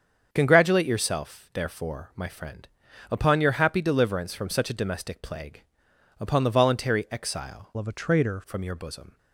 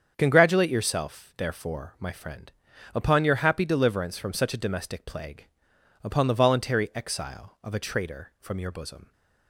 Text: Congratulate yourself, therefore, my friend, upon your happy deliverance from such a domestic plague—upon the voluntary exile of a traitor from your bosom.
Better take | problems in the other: second | starts louder than the rest; strong; until 1.3 s; 7 dB; strong in the second // changes voice from "of" to "traitor"; from 7.7 to 8.4 s; 0.7 s long

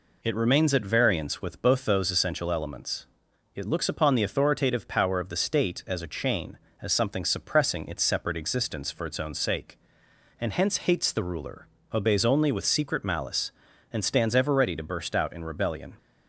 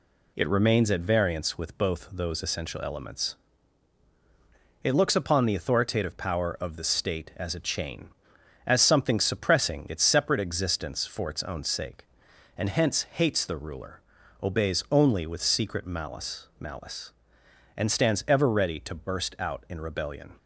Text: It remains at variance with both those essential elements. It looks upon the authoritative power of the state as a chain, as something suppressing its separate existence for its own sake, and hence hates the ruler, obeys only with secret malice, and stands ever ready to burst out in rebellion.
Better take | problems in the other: first | says "malice" twice; at 16.5 s

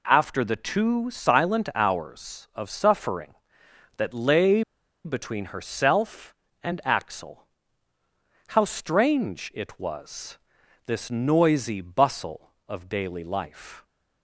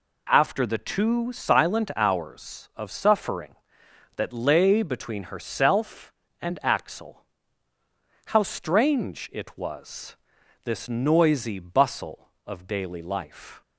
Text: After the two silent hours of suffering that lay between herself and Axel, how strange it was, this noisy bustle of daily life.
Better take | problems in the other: second | pauses between "lay" and "between"; at 4.6 s; 0.42 s long

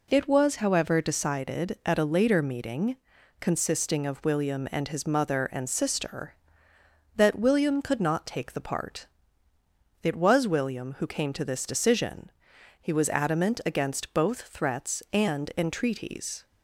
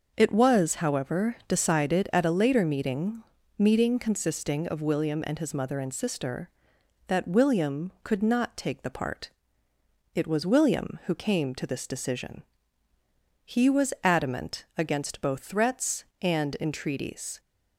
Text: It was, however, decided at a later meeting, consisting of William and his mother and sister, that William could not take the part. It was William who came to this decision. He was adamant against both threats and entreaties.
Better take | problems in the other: first | says "meeting" twice; at 3.5 s

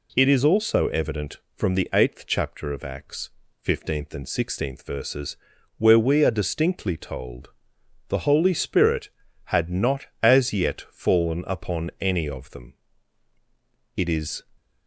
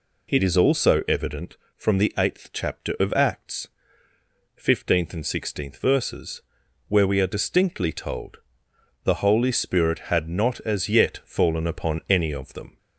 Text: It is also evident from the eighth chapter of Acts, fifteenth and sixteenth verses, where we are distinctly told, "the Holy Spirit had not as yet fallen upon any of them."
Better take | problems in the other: second | goes on to say "It is"; slight; from 13.9 s on; 0.48 s long

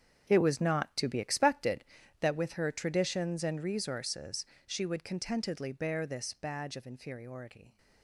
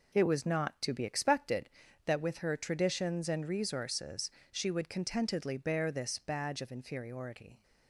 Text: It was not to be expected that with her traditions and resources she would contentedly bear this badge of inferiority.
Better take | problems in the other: second | gets quieter; strong; throughout; 13 dB // pauses between "resources" and "she"; slight; at 4.4 s; 0.20 s long; slight in the second

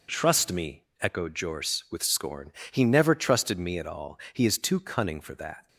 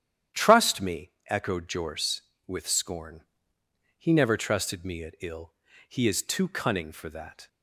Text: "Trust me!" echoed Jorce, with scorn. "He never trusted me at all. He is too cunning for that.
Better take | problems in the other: first | starts louder than the rest; strong; until 1.5 s; 10 dB // says "ill" for "all"; at 5.1 s

